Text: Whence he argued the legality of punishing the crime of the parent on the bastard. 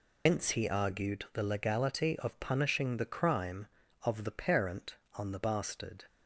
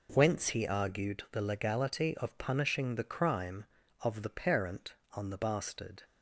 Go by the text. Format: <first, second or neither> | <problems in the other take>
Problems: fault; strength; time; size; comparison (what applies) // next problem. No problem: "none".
second | loses the start of "Whence"; at 0.2 s; 140 ms